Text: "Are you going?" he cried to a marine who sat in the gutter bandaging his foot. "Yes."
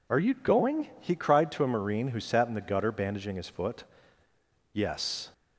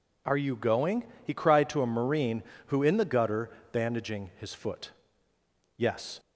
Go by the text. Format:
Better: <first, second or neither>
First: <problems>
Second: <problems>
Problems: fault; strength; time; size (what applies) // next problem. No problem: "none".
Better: first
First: none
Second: skips "sat"; at 2.8 s // pauses between "gutter" and "bandaging"; slight; at 3.4 s; 0.22 s long